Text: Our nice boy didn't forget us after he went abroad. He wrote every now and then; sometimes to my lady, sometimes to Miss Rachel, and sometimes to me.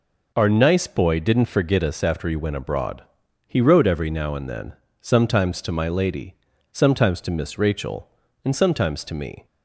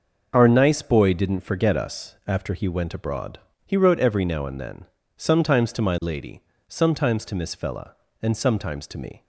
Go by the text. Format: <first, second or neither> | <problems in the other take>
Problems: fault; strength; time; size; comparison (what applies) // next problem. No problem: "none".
first | says "Fella" for "Rachel"; at 7.5 s